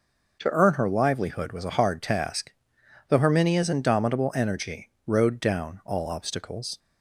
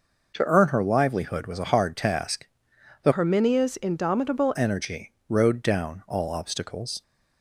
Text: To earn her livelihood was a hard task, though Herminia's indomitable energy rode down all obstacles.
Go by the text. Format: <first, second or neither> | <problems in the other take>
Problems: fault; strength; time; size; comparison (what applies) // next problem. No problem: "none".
first | changes voice from "Herminia's" to "indomitable"; from 3.1 to 4.5 s; 1.4 s long // pauses between "energy" and "rode"; slight; at 5.1 s; 0.16 s long; slight in the first